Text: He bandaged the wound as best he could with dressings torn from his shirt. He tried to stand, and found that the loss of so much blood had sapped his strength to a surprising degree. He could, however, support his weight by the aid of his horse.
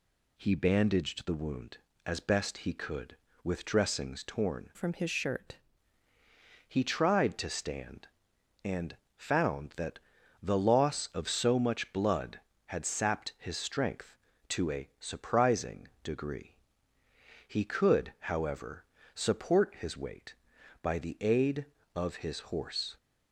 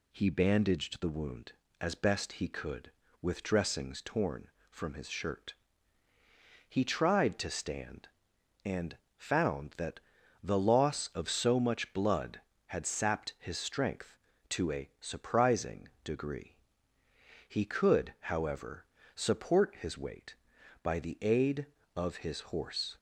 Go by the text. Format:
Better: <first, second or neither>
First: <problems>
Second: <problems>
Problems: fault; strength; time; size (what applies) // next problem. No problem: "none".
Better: second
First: changes voice from "from" to "shirt"; from 4.7 to 5.5 s; 0.8 s long // pauses between "and" and "found"; slight; at 8.9 s; 0.20 s long // pauses between "that" and "the"; at 9.9 s; 0.42 s long // pauses between "surprising" and "degree"; slight; at 15.8 s; 0.16 s long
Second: pauses between "and" and "found"; slight; at 8.9 s; 0.20 s long // pauses between "that" and "the"; at 9.9 s; 0.42 s long // pauses between "surprising" and "degree"; slight; at 15.8 s; 0.16 s long